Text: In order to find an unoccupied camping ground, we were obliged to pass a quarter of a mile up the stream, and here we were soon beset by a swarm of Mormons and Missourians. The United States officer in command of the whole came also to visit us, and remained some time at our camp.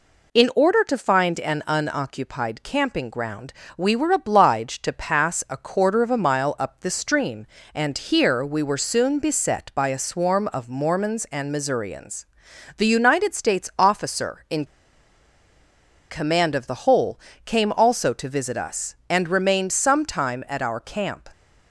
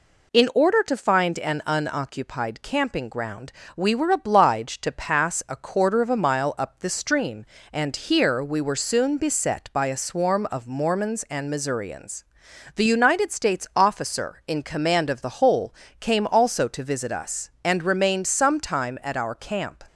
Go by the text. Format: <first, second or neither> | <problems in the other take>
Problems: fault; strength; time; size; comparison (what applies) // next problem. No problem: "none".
second | pauses between "in" and "command"; strong; at 14.6 s; 1.4 s long // pauses between "whole" and "came"; slight; at 17.1 s; 0.28 s long; slight in the second